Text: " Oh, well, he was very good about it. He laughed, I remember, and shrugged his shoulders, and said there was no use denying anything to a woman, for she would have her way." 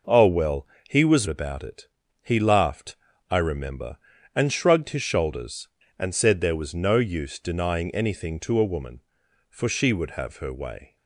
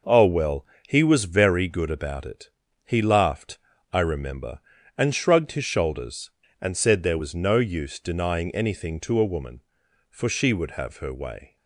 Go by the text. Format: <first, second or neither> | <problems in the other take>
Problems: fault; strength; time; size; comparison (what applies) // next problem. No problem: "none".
second | skips "very good"; at 1.2 s